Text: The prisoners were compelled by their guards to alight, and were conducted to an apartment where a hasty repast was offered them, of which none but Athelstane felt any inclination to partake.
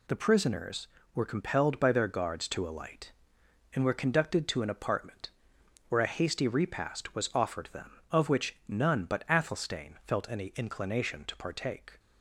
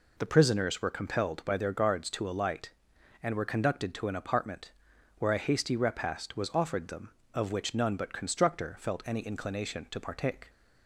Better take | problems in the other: first | pauses between "apartment" and "where"; noticeable; at 4.7 s; 0.48 s long; noticeable in the first // says "Constructor" for "Athelstane"; at 8.1 s

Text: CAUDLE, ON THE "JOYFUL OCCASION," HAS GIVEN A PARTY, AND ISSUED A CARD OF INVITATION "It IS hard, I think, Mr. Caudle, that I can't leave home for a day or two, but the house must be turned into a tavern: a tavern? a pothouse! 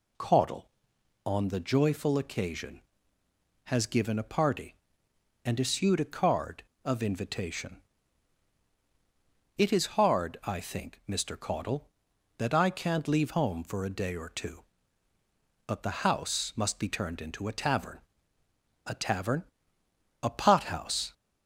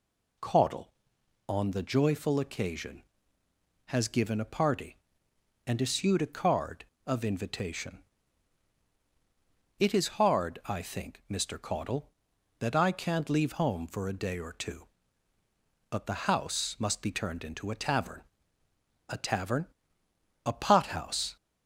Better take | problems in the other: neither | pauses between "INVITATION" and "It"; strong; the same in both

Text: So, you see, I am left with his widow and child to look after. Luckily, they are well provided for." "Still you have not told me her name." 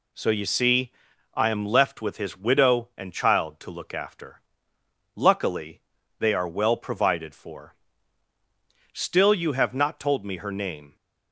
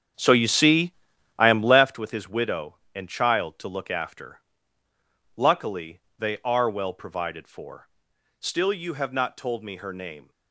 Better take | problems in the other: first | starts louder than the rest; strong; until 2.0 s; 8.5 dB

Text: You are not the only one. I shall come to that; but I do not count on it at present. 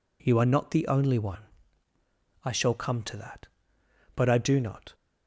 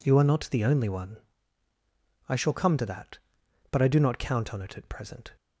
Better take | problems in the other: second | stops before "count on it at present"; at 4.9 s

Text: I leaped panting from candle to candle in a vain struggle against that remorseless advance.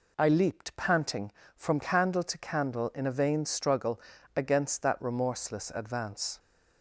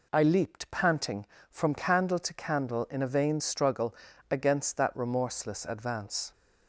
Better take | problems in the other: neither | pauses between "struggle" and "against"; slight; the same in both

